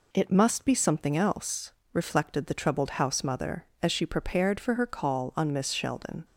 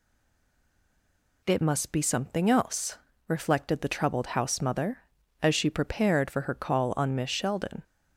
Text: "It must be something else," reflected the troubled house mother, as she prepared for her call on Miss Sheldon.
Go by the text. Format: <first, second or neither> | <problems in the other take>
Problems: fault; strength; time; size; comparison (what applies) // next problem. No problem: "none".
first | stays silent before the first word; noticeable; until 1.4 s; 1.4 s long